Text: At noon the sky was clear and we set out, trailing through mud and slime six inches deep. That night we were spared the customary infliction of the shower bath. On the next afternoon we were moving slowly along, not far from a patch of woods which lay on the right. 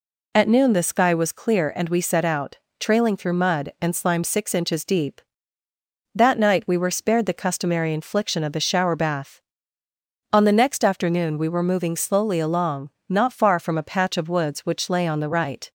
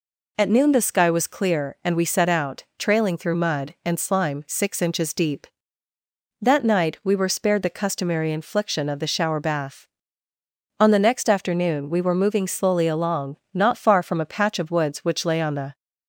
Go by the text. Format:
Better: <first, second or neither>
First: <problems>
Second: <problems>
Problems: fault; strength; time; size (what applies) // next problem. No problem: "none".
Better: first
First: none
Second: stops before "right"; at 15.7 s